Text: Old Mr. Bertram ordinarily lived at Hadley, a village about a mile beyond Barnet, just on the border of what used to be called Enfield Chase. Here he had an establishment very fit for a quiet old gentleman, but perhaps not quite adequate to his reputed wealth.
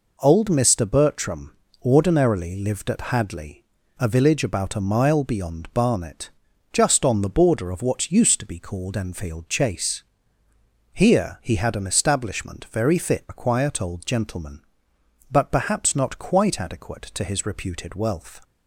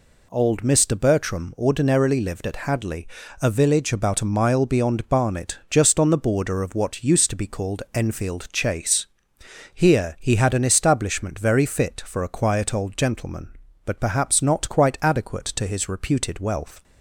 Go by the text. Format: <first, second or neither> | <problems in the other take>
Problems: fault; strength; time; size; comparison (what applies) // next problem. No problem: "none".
second | pauses between "Bertram" and "ordinarily"; slight; at 1.5 s; 0.26 s long // skips "for"; at 13.2 s